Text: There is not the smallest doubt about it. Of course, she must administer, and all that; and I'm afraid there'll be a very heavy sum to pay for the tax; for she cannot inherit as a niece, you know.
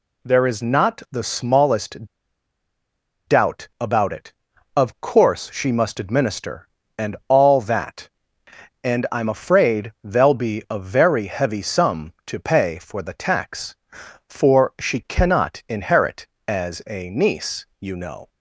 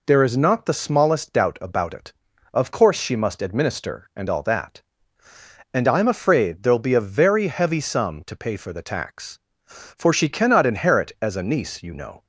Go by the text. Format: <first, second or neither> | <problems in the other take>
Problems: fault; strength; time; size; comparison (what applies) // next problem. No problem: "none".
second | pauses between "smallest" and "doubt"; at 2.0 s; 1.1 s long